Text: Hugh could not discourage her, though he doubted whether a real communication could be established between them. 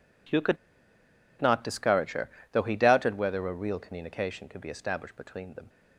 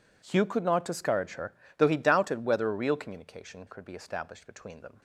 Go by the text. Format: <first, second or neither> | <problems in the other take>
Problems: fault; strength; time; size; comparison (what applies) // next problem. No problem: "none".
second | pauses between "could" and "not"; noticeable; at 0.5 s; 0.85 s long